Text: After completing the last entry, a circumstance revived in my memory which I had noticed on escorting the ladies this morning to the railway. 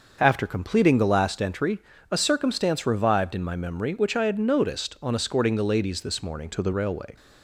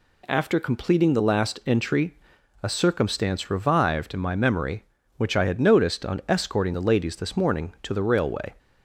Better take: second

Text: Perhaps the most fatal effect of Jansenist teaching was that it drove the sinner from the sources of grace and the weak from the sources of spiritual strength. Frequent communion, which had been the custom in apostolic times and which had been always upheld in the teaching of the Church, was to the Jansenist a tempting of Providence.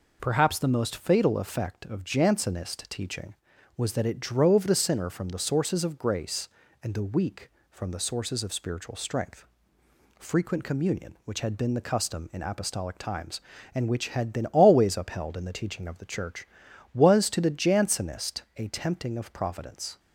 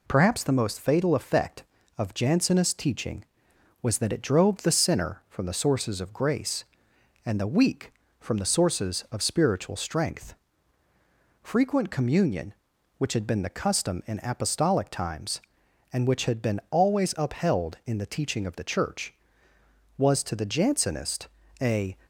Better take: first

